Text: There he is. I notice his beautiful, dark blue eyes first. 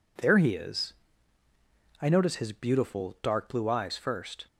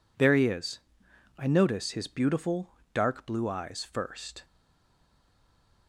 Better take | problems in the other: first | stays silent after the last word; noticeable; from 4.4 s on; 1.4 s long

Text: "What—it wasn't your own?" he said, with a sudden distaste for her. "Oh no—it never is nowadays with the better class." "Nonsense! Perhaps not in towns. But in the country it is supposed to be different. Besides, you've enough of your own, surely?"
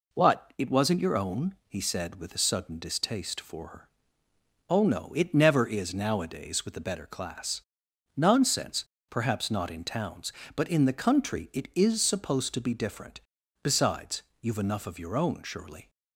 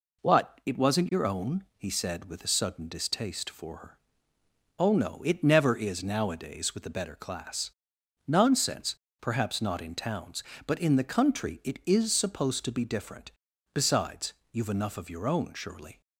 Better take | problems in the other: neither | none

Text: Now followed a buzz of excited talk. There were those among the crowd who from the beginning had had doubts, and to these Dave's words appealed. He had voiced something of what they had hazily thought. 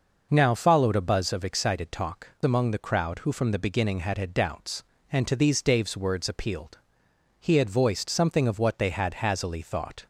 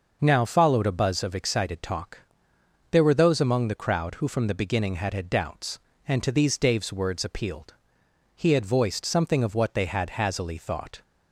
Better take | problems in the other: second | skips "There were those"; at 2.3 s

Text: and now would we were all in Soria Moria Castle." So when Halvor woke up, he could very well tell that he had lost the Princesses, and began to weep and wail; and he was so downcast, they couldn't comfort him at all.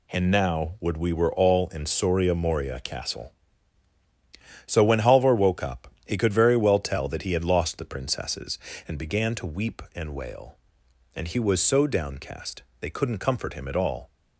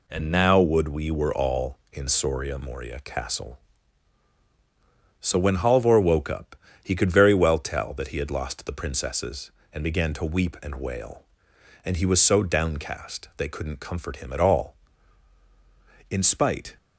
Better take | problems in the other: first | goes on to say "In spite"; noticeable; from 16.0 s on; 0.68 s long

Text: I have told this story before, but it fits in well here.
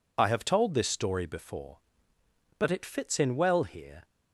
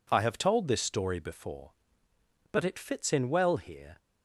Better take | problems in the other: second | loses the start of "I"; at 0.1 s; 40 ms

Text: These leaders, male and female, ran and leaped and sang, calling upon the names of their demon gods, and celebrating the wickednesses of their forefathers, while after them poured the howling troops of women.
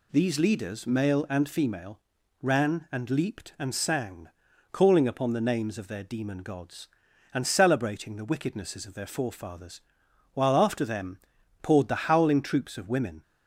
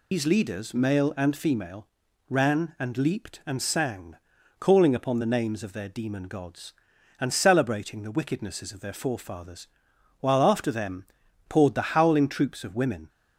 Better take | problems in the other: first | loses the start of "These"; at 0.1 s; 125 ms // pauses between "them" and "poured"; at 11.0 s; 0.44 s long; also in the first

